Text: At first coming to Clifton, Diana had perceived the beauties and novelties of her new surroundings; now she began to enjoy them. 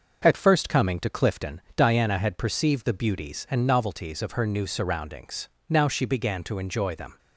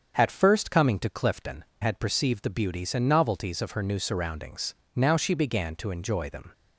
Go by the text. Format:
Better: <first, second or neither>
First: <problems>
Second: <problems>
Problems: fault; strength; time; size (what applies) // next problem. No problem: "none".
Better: first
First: starts louder than the rest; noticeable; until 1.2 s; 6 dB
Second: starts louder than the rest; strong; until 1.2 s; 7 dB // skips "Diana"; at 1.7 s